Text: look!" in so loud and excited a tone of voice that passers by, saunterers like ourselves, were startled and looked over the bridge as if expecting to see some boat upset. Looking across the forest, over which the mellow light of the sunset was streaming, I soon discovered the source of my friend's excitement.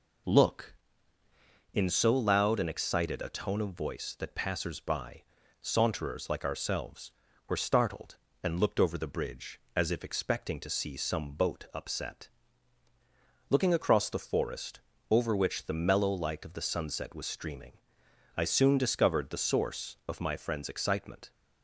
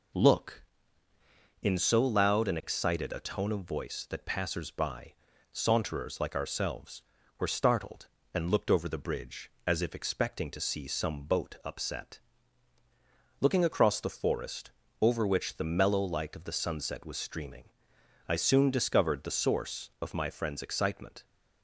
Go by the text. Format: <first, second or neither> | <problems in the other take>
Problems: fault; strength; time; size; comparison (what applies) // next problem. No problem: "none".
neither | none